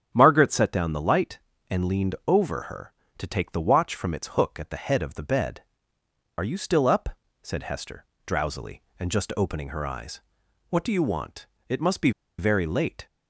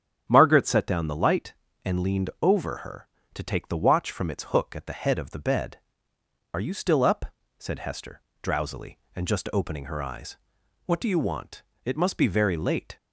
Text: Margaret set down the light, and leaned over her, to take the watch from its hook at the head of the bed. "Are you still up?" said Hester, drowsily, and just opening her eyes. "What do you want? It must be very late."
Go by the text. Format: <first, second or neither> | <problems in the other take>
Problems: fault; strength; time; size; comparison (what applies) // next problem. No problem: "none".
second | starts louder than the rest; strong; until 1.1 s; 9 dB; strong in the second // pauses between "be" and "very"; slight; at 12.1 s; 0.28 s long